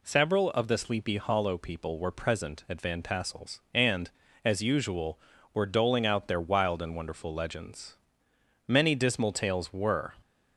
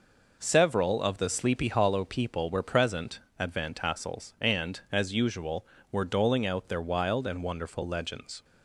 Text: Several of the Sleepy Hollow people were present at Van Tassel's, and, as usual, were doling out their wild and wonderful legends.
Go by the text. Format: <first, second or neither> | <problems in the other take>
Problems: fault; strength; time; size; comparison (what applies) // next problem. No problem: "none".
second | goes on to say "Many dismal tales were"; from 8.6 s on; 1.4 s long